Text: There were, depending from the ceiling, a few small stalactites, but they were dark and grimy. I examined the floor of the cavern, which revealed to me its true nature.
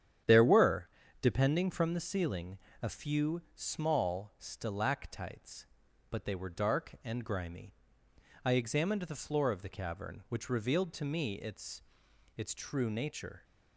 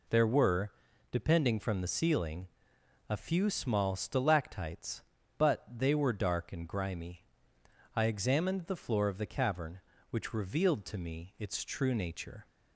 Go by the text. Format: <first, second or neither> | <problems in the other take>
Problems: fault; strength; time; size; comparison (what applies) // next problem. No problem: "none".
second | starts louder than the rest; strong; until 1.5 s; 9.5 dB // says "its" twice; at 12.3 s